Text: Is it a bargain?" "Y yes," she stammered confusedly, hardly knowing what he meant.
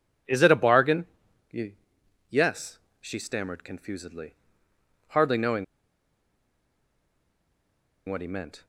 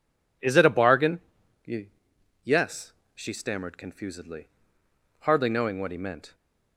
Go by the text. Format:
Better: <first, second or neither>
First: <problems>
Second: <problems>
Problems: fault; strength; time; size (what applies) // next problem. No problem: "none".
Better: second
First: pauses between "Y" and "yes"; noticeable; at 1.7 s; 0.58 s long // pauses between "knowing" and "what"; strong; at 5.6 s; 2.4 s long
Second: pauses between "Y" and "yes"; noticeable; at 1.8 s; 0.58 s long